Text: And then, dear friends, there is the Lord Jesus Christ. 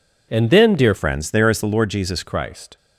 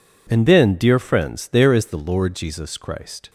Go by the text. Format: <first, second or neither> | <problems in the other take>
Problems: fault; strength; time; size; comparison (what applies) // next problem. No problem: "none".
second | changes voice from "friends" to "Jesus"; from 0.9 to 2.2 s; 1.3 s long